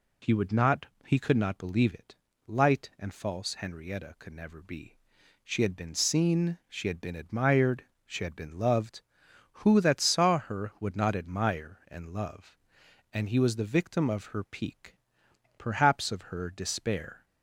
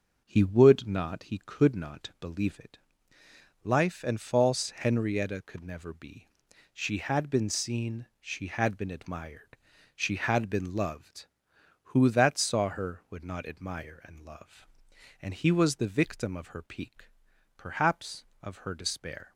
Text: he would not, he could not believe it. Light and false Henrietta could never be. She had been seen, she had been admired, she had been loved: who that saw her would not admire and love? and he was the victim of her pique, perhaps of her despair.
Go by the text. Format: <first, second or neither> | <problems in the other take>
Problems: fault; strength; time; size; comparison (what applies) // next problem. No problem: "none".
first | starts louder than the rest; until 1.2 s; 6.5 dB // says "Life" for "Light"; at 3.6 s